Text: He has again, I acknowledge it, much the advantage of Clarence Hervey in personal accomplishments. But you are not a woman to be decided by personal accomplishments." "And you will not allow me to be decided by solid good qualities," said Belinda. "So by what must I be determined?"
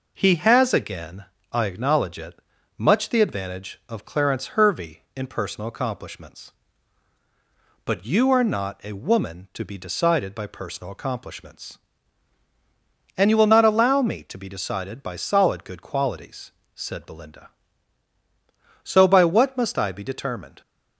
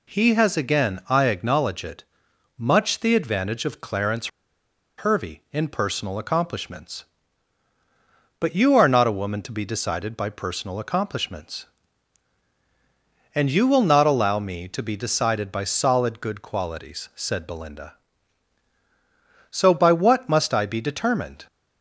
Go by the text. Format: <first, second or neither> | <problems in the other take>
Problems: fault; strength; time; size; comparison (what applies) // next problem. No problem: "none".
first | pauses between "Clarence" and "Hervey"; noticeable; at 4.2 s; 0.69 s long